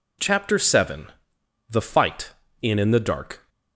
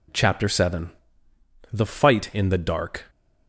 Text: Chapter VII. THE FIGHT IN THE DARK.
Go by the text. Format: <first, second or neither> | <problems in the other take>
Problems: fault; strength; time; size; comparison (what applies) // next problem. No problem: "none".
second | says "IN" twice; at 2.7 s